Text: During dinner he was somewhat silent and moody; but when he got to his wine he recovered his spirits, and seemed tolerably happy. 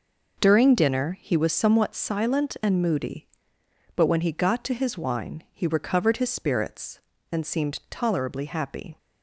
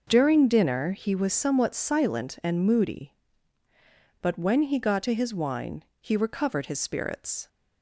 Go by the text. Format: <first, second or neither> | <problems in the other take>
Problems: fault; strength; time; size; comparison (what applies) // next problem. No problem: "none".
first | pauses between "wine" and "he"; slight; at 5.8 s; 0.16 s long // stops before "and seemed tolerably happy"; at 7.4 s